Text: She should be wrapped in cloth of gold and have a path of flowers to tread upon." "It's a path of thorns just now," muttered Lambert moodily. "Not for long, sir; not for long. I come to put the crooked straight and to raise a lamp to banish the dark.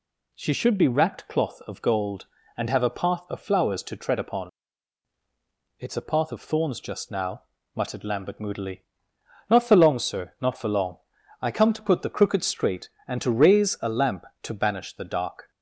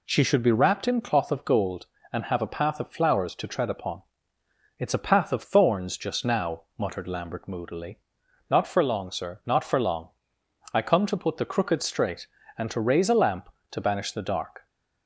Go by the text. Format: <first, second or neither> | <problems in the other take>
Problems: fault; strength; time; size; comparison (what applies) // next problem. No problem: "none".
second | skips "in"; at 1.2 s